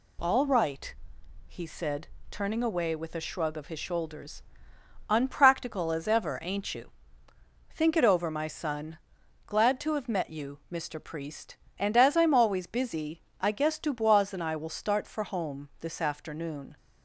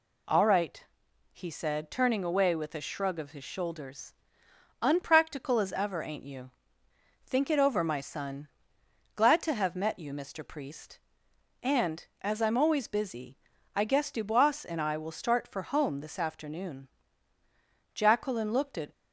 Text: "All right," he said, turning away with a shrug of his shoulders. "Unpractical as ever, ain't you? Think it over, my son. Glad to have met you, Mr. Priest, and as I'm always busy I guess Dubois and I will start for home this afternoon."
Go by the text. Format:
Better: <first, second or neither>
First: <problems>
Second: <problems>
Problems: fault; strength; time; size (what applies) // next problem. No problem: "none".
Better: first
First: pauses between "busy" and "I"; slight; at 13.2 s; 0.18 s long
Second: pauses between "busy" and "I"; slight; at 13.3 s; 0.36 s long // goes on to say "Jacqueline looked at"; noticeable; from 17.9 s on; 0.96 s long